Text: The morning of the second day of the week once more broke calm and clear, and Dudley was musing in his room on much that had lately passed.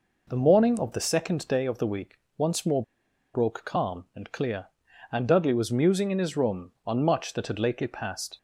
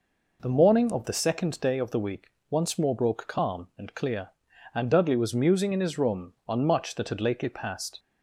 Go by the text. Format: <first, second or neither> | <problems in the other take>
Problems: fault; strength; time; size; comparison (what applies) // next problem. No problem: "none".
second | pauses between "week" and "once"; slight; at 2.1 s; 0.18 s long; slight in the second // pauses between "more" and "broke"; noticeable; at 2.8 s; 0.51 s long